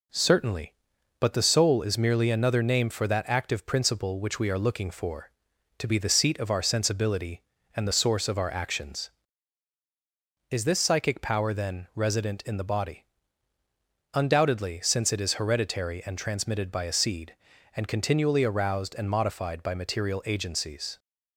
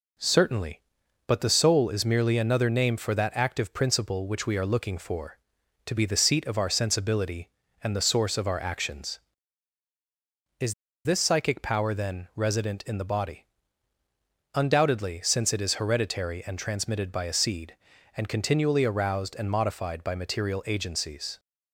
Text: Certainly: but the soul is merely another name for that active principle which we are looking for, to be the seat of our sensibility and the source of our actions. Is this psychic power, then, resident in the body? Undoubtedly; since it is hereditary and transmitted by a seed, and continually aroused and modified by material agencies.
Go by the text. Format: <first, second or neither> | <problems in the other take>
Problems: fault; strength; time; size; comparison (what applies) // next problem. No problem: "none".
first | pauses between "Is" and "this"; slight; at 10.7 s; 0.31 s long